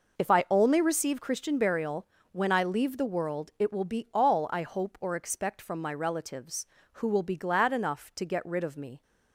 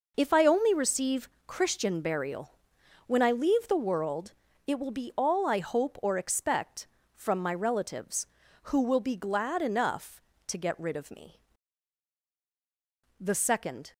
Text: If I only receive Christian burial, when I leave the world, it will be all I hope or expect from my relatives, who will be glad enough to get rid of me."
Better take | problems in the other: first | pauses between "receive" and "Christian"; slight; at 1.2 s; 0.18 s long // goes on to say "The second"; noticeable; from 13.1 s on; 0.74 s long

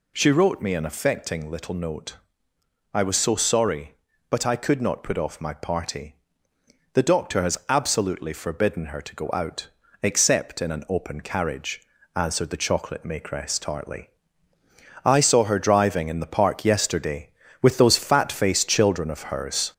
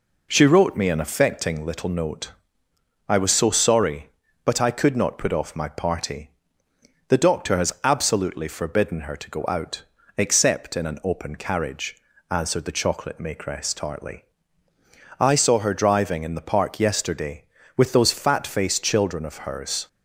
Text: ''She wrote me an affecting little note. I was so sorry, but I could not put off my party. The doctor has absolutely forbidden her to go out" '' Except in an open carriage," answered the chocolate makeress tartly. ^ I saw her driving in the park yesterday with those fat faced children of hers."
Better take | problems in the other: second | gets louder; noticeable; throughout; 4 dB

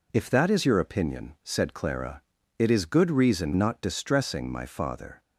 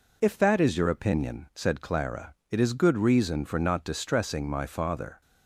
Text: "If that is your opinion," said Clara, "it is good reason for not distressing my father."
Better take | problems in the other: second | skips "for"; at 3.5 s

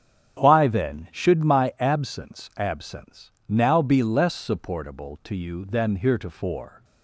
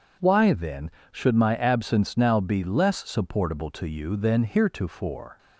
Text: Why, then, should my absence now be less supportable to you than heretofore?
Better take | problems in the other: second | starts louder than the rest; strong; until 1.4 s; 8.5 dB // says "absence" twice; at 2.5 s

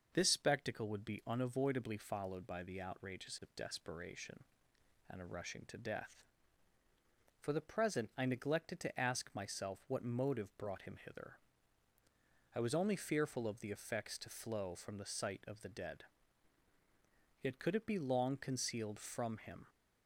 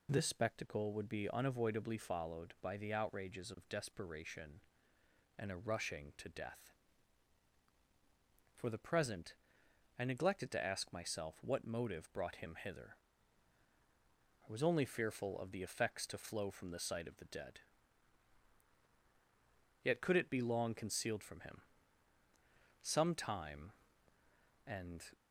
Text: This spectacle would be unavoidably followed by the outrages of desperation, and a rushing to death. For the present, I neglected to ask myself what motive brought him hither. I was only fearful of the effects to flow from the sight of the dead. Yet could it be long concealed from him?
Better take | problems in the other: first | goes on to say "Some time and"; strong; from 22.8 s on; 2.2 s long

